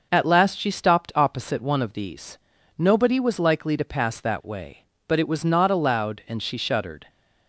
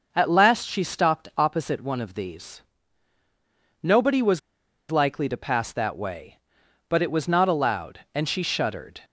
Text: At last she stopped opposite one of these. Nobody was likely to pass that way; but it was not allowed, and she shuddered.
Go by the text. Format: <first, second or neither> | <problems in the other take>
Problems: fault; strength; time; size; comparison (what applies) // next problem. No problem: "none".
first | pauses between "was" and "likely"; noticeable; at 4.3 s; 0.51 s long